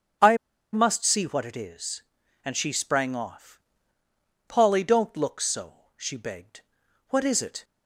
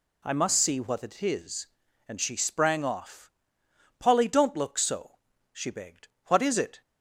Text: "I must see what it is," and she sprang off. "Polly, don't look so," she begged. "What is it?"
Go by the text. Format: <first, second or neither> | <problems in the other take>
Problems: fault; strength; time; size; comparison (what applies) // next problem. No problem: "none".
second | starts louder than the rest; strong; until 1.5 s; 7.5 dB // pauses between "I" and "must"; at 0.3 s; 0.36 s long